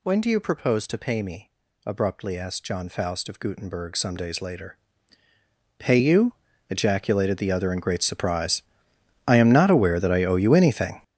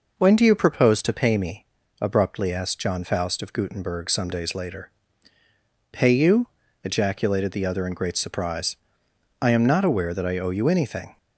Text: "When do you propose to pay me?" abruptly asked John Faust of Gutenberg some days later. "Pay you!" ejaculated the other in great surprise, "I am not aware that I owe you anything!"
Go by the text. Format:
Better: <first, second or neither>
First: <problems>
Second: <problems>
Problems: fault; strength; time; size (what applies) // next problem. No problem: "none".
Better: second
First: gets louder; strong; throughout; 12.5 dB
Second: none